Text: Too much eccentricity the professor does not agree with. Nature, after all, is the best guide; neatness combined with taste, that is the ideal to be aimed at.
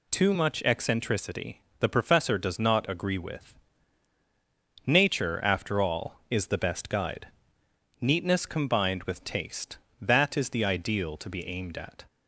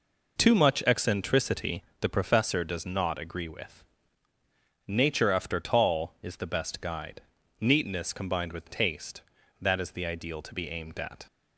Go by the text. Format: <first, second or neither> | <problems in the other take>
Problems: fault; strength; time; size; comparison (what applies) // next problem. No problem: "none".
first | pauses between "eccentricity" and "the"; slight; at 1.8 s; 0.18 s long; slight in the first // says "tall" for "all"; at 5.5 s